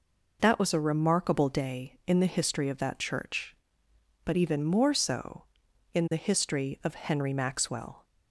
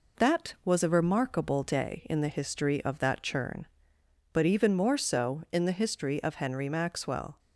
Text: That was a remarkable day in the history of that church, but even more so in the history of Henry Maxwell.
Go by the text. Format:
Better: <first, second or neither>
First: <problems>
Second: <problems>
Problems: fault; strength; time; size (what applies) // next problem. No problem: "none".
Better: first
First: none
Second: says "churn" for "church"; at 3.2 s